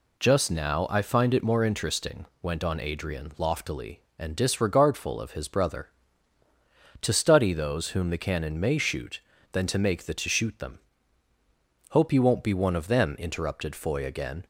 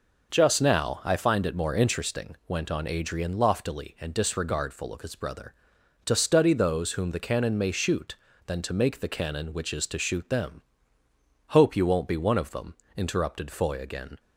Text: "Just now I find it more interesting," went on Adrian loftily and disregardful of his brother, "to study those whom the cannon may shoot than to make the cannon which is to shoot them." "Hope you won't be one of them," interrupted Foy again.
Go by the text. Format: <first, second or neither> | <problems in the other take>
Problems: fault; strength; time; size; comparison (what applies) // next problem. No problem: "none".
second | skips "cannon which is"; at 10.1 s